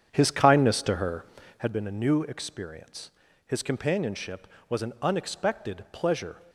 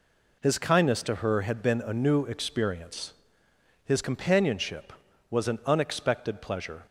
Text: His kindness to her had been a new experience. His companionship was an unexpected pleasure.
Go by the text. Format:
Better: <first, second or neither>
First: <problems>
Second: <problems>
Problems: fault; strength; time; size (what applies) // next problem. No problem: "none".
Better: second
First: starts louder than the rest; strong; until 1.7 s; 8 dB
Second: none